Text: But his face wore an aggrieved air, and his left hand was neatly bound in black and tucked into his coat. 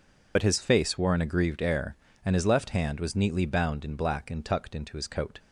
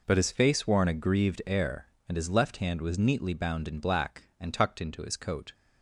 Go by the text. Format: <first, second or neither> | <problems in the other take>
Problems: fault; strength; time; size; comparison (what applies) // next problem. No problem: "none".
second | loses the start of "But"; at 0.3 s; 65 ms